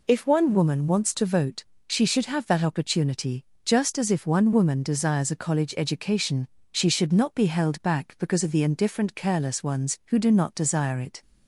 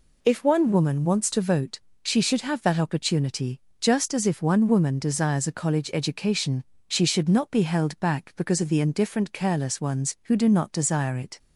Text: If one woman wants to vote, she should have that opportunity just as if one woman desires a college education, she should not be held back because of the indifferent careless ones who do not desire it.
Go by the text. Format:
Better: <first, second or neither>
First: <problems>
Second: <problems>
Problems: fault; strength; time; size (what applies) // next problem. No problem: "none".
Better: neither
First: pauses between "opportunity" and "just"; slight; at 3.4 s; 0.20 s long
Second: pauses between "opportunity" and "just"; slight; at 3.6 s; 0.20 s long